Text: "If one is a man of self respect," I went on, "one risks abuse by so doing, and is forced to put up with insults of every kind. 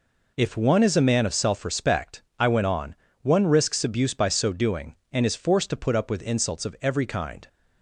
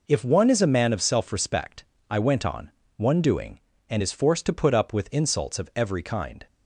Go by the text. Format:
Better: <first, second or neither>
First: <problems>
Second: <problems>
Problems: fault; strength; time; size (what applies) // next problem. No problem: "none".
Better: first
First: none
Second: skips "risks abuse by so"; at 3.2 s